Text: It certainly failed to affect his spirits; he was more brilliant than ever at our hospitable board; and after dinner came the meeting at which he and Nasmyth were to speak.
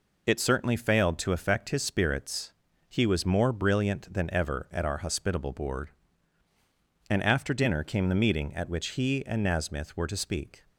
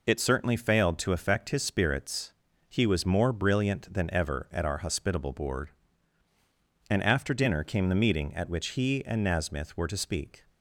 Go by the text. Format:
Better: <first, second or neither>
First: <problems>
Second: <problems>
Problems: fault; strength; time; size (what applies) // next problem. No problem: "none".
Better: neither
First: none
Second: none